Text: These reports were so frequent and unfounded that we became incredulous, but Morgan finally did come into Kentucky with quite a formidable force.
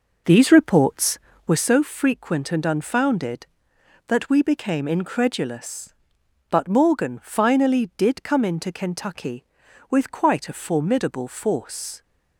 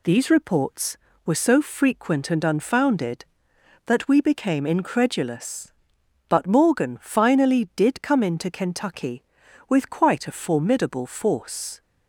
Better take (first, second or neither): second